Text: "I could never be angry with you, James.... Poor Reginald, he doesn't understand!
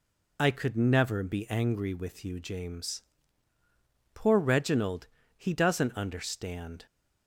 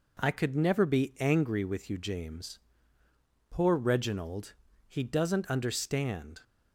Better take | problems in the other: second | loses the start of "I"; at 0.3 s; 45 ms

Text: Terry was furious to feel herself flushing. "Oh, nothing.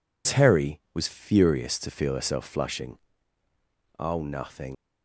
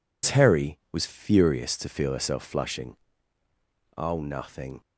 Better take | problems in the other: second | leaves "nothing" unfinished; at 4.7 s; 70 ms

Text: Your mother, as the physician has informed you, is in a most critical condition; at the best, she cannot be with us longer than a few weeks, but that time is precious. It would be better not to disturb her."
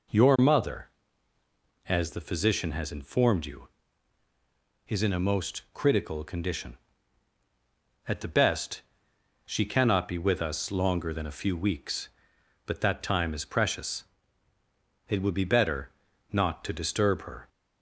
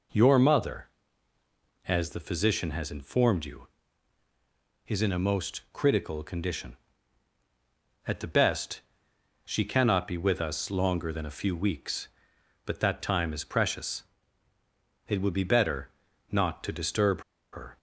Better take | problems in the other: first | pauses between "better" and "not"; at 15.8 s; 0.42 s long; also in the first // pauses between "disturb" and "her"; slight; at 17.2 s; 0.31 s long

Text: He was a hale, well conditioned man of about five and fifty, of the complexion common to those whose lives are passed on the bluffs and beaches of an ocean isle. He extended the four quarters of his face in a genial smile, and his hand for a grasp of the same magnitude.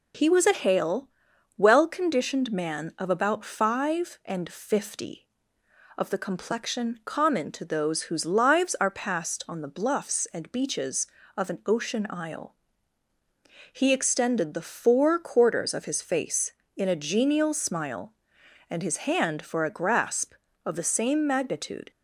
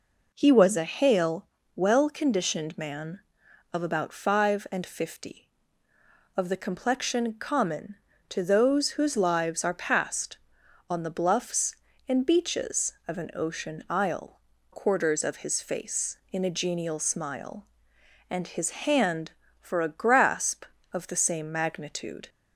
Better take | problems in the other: first | skips "He extended the four"; at 14.5 s

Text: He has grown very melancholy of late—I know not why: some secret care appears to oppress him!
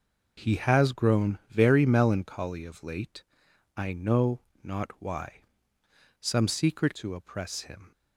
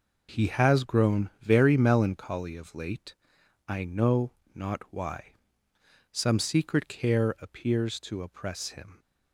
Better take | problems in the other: second | pauses between "know" and "not"; slight; at 4.3 s; 0.24 s long; slight in the second // skips "care appears"; at 6.9 s

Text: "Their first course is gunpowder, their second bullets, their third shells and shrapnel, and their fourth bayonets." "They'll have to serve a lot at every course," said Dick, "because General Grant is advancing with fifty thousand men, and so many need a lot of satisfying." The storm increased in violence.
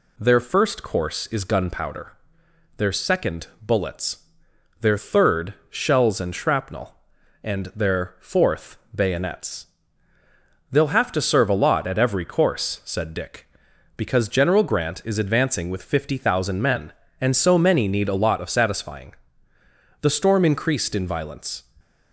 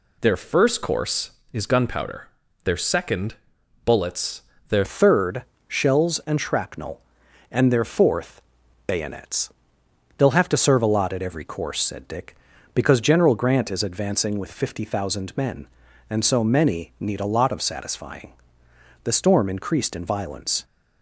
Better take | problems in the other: first | pauses between "second" and "bullets"; noticeable; at 3.3 s; 0.50 s long // changes voice at "third"; from 4.8 s on; 15.8 s long // pauses between "third" and "shells"; slight; at 5.4 s; 0.24 s long; slight in the first // pauses between "fourth" and "bayonets"; noticeable; at 8.4 s; 0.48 s long; slight in the first

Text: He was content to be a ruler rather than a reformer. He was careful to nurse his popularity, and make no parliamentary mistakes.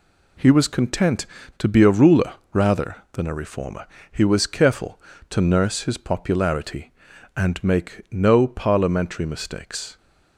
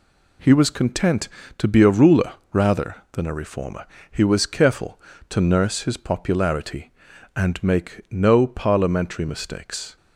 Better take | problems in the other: neither | pauses between "ruler" and "rather"; slight; the same in both

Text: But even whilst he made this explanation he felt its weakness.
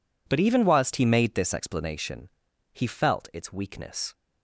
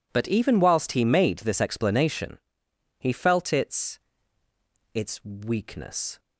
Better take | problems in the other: first | pauses between "explanation" and "he"; noticeable; at 2.3 s; 0.62 s long; also in the first // says "its" twice; at 4.9 s

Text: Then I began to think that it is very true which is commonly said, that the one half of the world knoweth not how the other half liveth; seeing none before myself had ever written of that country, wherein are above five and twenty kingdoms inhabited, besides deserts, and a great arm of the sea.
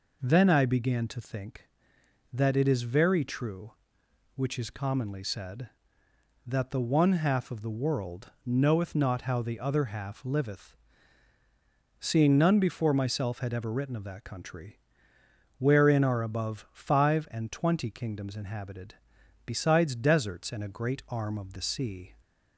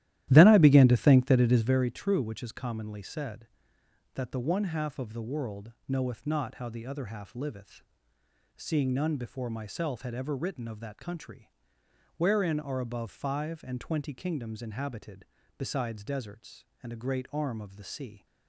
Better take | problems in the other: first | starts louder than the rest; strong; until 1.9 s; 13.5 dB // pauses between "world" and "knoweth"; slight; at 5.7 s; 0.16 s long; slight in the first

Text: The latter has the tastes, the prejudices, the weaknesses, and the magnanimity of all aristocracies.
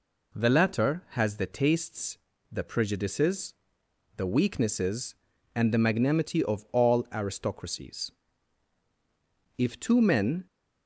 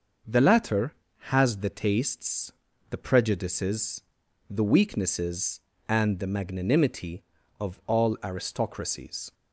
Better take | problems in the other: second | goes on to say "If two men"; noticeable; from 9.5 s on; 0.88 s long

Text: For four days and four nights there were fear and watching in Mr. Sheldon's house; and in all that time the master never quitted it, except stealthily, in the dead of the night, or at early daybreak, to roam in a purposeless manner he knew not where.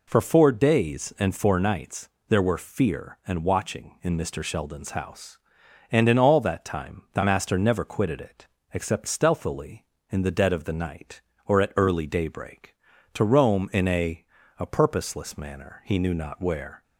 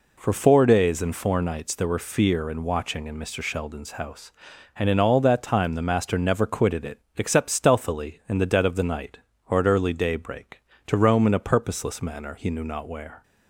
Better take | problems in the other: second | pauses between "nights" and "there"; slight; at 2.0 s; 0.20 s long // says "a" twice; at 14.5 s

